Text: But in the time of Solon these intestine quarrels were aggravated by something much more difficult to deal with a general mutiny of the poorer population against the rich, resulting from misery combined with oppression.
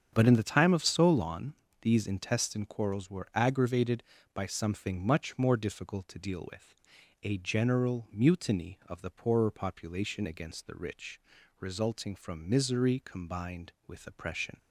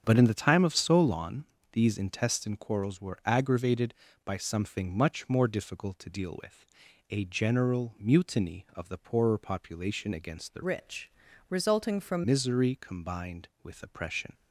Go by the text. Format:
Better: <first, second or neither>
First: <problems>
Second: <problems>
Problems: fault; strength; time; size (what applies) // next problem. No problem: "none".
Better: first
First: starts louder than the rest; strong; until 1.1 s; 7.5 dB // pauses between "Solon" and "these"; slight; at 1.5 s; 0.28 s long // pauses between "with" and "a"; noticeable; at 6.7 s; 0.49 s long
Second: starts louder than the rest; strong; until 1.0 s; 7.5 dB // pauses between "Solon" and "these"; slight; at 1.4 s; 0.28 s long // pauses between "with" and "a"; noticeable; at 6.6 s; 0.46 s long // changes voice from "rich" to "from"; from 10.6 to 12.2 s; 1.6 s long